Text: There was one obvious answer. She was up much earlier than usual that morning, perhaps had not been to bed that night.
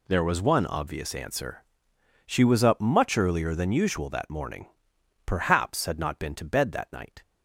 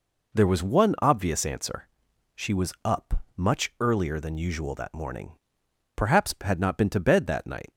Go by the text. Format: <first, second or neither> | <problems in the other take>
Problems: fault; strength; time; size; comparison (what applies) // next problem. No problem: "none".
neither | none